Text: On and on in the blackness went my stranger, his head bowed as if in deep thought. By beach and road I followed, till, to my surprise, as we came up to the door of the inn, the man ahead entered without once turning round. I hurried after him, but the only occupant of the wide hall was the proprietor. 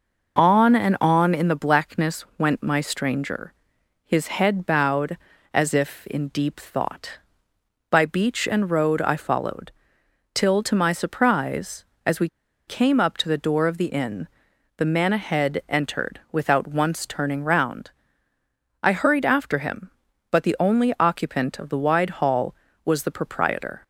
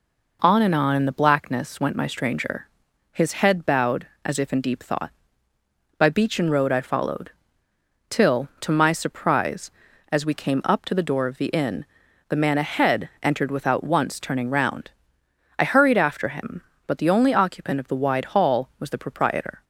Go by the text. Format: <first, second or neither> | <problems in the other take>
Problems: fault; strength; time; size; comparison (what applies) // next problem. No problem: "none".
second | pauses between "we" and "came"; at 12.2 s; 0.38 s long